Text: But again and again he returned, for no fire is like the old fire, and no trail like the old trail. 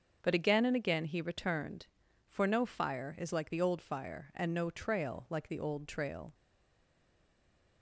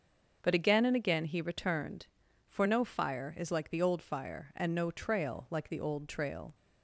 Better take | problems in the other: second | starts louder than the rest; until 1.2 s; 7 dB; also in the second // stays silent after the last word; noticeable; from 6.3 s on; 1.5 s long

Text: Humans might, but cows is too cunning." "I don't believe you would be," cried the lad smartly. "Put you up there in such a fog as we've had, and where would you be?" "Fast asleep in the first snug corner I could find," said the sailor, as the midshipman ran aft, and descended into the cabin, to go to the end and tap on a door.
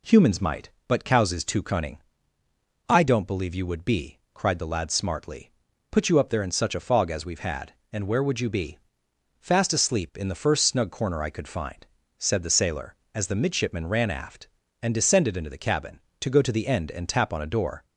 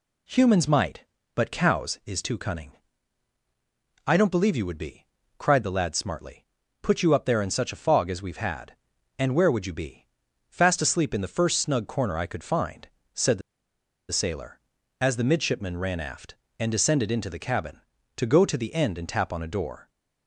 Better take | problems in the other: first | pauses between "the" and "sailor"; noticeable; at 13.4 s; 0.70 s long

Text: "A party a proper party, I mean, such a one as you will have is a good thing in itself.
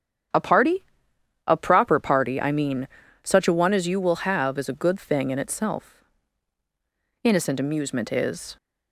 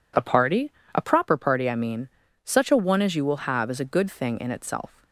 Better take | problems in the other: second | starts louder than the rest; strong; until 1.9 s; 9 dB // pauses between "party" and "a"; noticeable; at 0.8 s; 0.62 s long; slight in the second // goes on to say "Innocent amusement is"; from 7.2 s on; 1.3 s long

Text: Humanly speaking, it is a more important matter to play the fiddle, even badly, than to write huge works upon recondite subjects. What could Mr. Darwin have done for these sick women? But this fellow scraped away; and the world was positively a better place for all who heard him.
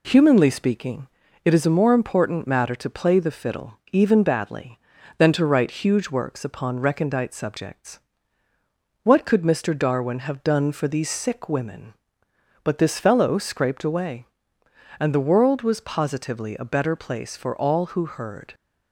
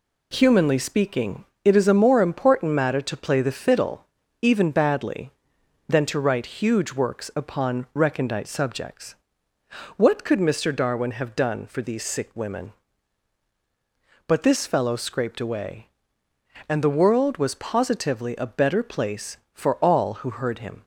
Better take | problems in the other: second | stops before "him"; at 18.5 s

